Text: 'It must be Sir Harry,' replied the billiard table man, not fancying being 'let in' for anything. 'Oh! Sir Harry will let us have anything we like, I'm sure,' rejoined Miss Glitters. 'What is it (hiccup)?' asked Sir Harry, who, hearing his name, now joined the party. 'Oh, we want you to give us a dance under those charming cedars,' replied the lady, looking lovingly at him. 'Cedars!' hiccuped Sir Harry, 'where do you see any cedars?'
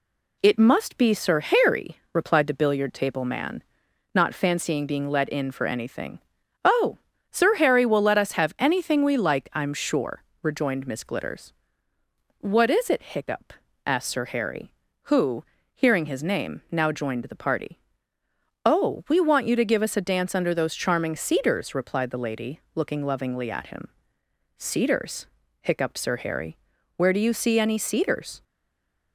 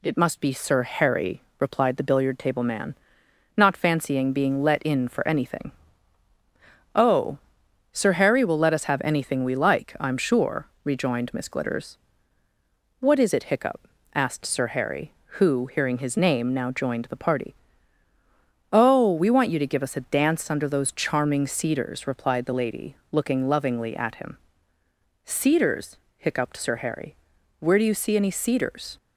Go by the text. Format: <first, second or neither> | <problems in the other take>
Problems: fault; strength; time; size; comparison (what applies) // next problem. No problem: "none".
second | stays silent after the last word; slight; from 28.4 s on; 0.7 s long